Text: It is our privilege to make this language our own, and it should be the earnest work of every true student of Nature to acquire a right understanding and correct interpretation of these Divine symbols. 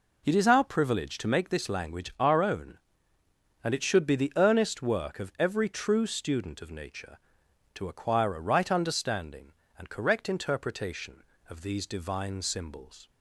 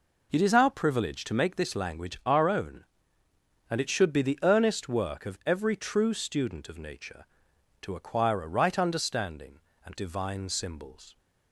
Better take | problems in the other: first | skips "correct interpretation of these"; at 9.9 s

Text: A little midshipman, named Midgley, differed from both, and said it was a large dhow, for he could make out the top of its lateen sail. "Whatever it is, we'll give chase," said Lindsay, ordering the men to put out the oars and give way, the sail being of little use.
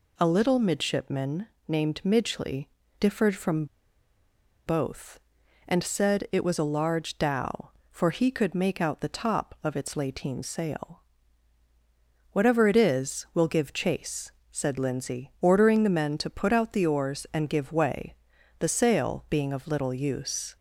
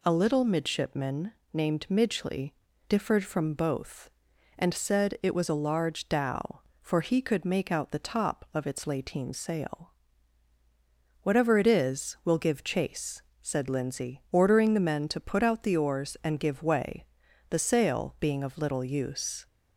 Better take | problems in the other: second | pauses between "from" and "both"; at 3.6 s; 1.0 s long

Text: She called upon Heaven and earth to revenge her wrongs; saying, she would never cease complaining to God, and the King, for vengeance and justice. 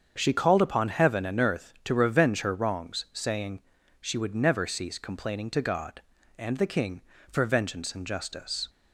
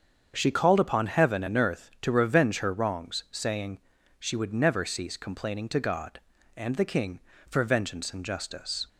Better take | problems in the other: neither | starts louder than the rest; strong; the same in both

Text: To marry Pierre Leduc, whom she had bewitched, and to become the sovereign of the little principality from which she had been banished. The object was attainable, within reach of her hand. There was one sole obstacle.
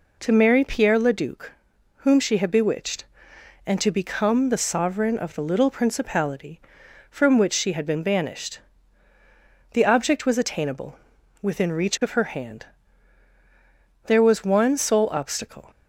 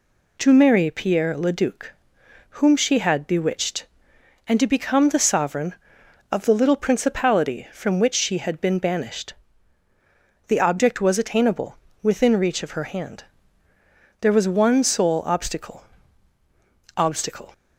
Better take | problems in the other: first | says "obstacle" twice; at 16.9 s

